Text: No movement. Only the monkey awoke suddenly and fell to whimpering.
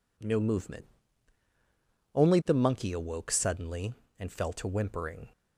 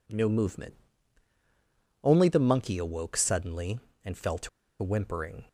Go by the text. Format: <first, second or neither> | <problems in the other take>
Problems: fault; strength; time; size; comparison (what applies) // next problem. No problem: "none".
first | pauses between "to" and "whimpering"; slight; at 4.4 s; 0.33 s long